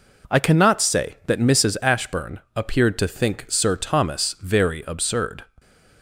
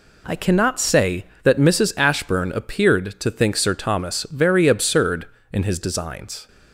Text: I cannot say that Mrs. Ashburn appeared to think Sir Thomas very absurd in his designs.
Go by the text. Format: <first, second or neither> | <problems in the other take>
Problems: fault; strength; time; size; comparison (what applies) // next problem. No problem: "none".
second | pauses between "Ashburn" and "appeared"; slight; at 2.3 s; 0.16 s long // stops before "in his designs"; at 5.5 s